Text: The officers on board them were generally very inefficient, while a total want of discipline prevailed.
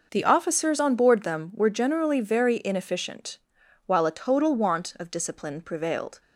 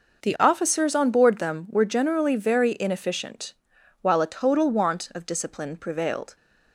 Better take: neither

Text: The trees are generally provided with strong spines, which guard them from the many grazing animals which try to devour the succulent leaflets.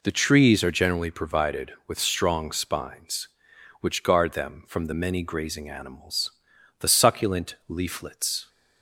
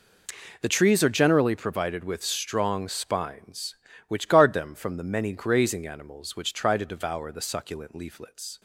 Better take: second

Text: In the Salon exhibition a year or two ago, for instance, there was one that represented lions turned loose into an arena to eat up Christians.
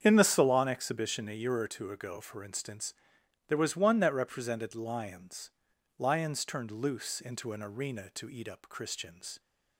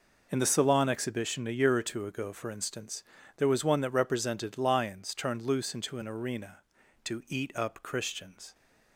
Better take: second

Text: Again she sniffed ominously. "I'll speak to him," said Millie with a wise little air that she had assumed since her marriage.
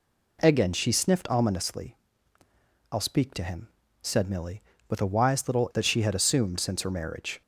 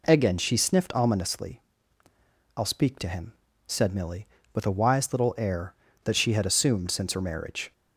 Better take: second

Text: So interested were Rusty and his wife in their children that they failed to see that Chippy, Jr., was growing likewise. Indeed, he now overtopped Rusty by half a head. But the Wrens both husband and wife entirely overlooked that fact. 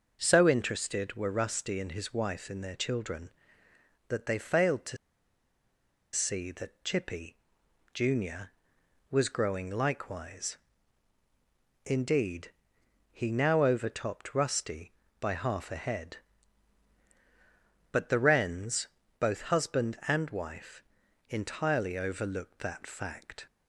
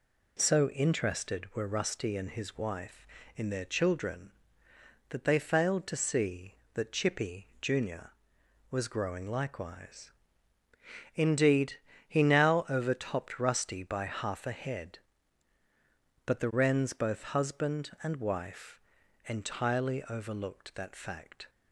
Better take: second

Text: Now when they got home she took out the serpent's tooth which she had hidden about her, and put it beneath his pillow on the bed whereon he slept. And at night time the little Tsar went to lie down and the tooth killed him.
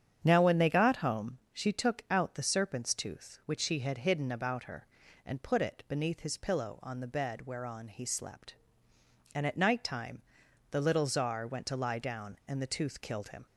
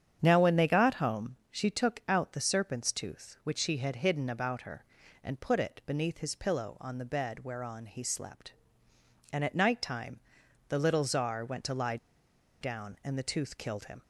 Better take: first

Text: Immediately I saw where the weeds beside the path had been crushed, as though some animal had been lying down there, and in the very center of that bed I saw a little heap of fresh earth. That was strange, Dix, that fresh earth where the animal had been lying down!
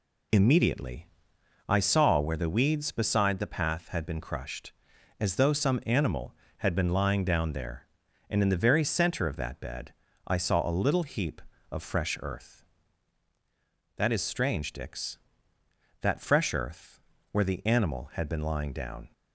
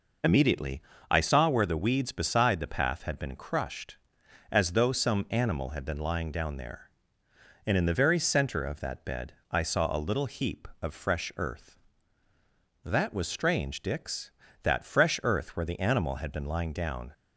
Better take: second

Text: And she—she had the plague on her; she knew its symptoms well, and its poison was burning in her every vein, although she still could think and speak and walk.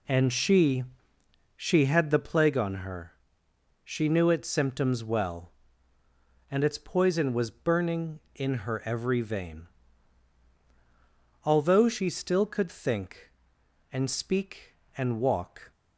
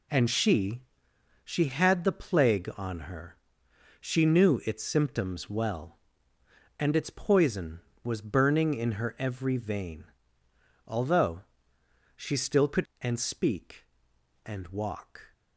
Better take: first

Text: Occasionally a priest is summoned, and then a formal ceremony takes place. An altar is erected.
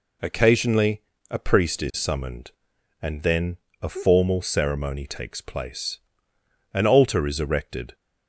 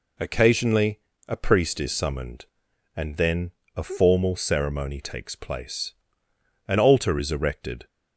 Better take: neither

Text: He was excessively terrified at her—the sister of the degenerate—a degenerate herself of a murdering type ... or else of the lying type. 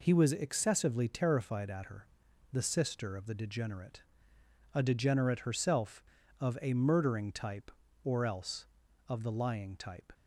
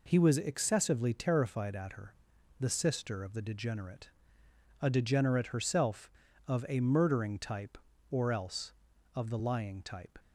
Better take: neither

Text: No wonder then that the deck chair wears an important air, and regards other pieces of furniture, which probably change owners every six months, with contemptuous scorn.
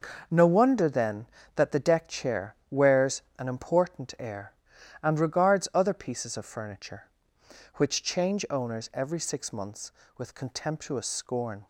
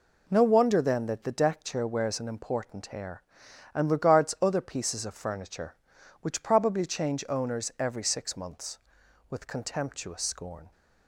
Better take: second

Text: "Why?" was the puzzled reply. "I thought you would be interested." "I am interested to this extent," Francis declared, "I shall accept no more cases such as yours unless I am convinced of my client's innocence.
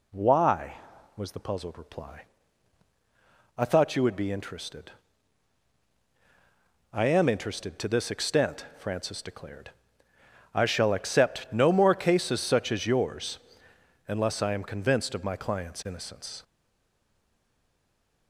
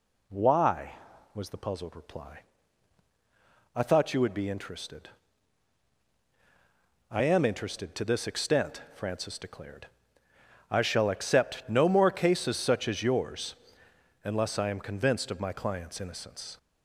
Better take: second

